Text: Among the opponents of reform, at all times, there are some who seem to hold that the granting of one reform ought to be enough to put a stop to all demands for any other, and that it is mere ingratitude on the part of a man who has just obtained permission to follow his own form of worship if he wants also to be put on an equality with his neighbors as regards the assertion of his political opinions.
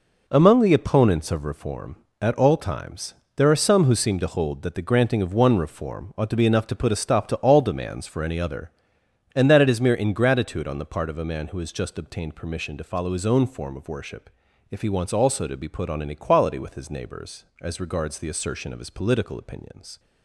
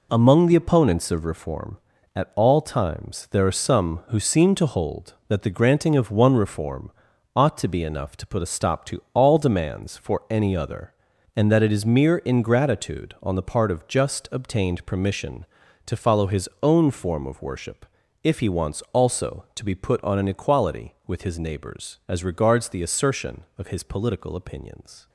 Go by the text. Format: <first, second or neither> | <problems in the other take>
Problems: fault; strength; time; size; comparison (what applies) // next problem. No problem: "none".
first | pauses between "reform" and "ought"; at 6.9 s; 0.44 s long // skips "a man who has"; at 13.8 s // pauses between "worship" and "if"; at 17.8 s; 0.38 s long; also in the first